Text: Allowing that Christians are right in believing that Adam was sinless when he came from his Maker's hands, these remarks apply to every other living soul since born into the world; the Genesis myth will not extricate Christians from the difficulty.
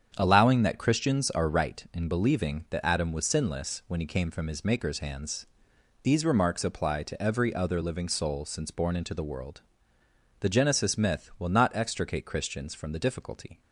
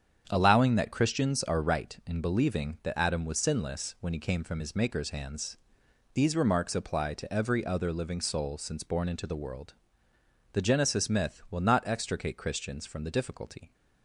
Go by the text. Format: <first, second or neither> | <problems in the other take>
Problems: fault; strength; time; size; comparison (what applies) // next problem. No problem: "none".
neither | starts louder than the rest; strong; the same in both